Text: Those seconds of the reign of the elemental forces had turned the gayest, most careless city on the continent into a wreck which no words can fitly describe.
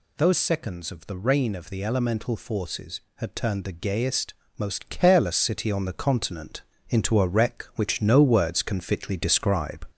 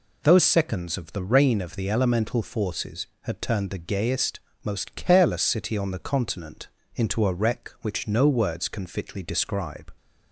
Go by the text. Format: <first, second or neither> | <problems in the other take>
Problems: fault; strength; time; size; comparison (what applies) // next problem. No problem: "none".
second | gets louder; slight; throughout; 3.5 dB // pauses between "continent" and "into"; slight; at 6.6 s; 0.26 s long; slight in the second